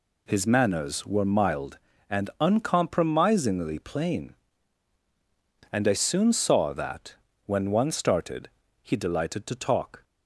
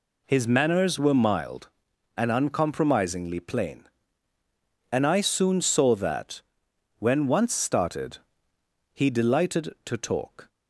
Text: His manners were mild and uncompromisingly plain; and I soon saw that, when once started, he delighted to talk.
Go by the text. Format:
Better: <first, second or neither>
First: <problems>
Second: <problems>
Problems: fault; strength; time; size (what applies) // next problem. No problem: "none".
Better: second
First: says "one" for "once"; at 7.7 s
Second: none